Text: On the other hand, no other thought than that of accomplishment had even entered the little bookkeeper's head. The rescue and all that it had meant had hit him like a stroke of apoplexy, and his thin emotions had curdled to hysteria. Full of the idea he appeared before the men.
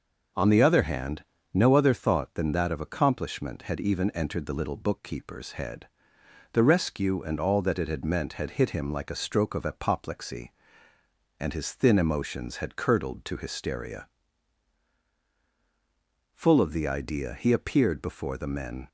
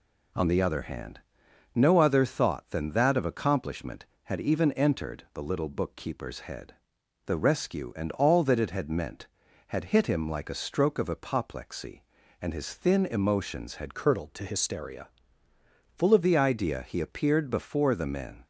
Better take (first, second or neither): first